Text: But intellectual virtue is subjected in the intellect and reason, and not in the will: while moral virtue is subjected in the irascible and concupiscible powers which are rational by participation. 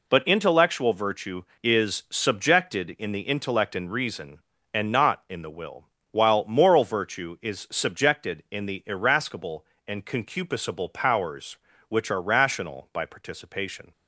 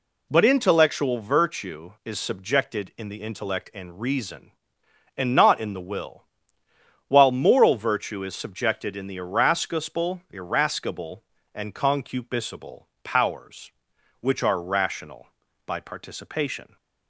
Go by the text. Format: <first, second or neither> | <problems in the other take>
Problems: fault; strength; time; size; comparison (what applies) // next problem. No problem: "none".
first | says "irascible" twice; at 10.2 s // pauses between "concupiscible" and "powers"; slight; at 12.8 s; 0.20 s long